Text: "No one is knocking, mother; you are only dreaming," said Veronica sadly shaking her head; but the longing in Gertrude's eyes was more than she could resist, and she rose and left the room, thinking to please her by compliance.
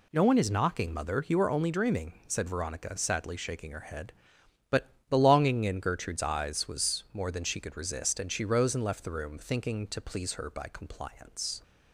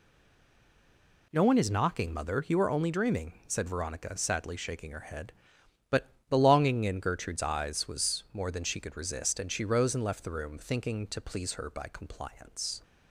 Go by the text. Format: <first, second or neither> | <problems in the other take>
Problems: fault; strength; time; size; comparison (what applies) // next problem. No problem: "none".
first | stays silent before the first word; noticeable; until 1.3 s; 1.3 s long // pauses between "but" and "the"; slight; at 6.0 s; 0.22 s long; slight in the first